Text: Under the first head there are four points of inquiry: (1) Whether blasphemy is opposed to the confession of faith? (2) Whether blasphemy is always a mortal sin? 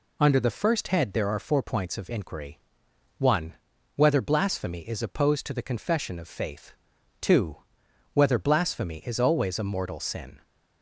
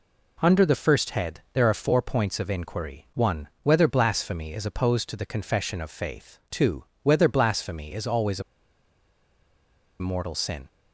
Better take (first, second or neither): first